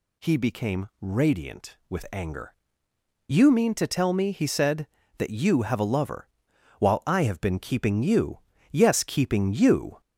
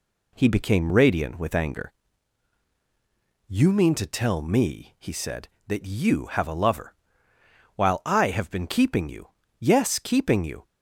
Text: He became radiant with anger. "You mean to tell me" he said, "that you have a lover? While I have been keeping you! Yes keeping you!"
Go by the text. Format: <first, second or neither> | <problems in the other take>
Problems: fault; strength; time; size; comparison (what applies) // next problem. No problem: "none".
second | gets louder; throughout; 3.5 dB